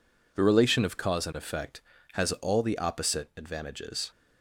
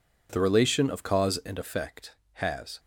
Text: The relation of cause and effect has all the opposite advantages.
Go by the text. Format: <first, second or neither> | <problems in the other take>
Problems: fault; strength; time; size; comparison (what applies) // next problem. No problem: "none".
first | stops before "all the opposite advantages"; at 2.7 s